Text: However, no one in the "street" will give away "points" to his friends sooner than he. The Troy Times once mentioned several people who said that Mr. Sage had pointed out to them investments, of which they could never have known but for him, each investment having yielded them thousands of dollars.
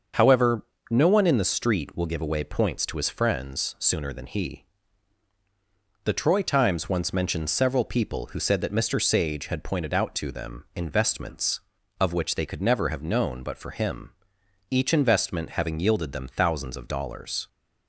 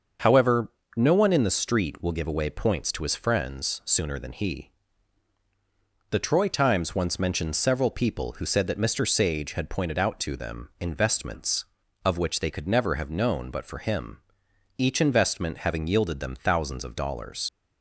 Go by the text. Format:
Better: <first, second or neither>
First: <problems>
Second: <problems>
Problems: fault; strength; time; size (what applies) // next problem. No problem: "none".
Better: first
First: starts louder than the rest; until 1.3 s; 6.5 dB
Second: starts louder than the rest; until 1.4 s; 6.5 dB // leaves "dollars" unfinished; at 17.4 s; 65 ms